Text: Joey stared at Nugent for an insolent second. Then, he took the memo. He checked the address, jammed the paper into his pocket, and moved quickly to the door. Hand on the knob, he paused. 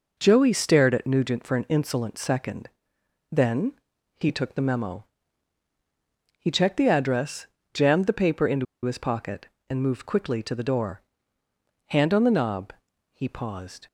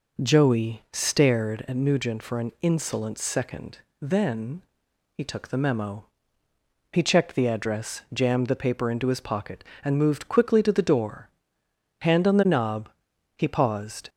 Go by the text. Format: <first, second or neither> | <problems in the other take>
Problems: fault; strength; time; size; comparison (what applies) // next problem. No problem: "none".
second | pauses between "into" and "his"; slight; at 8.6 s; 0.19 s long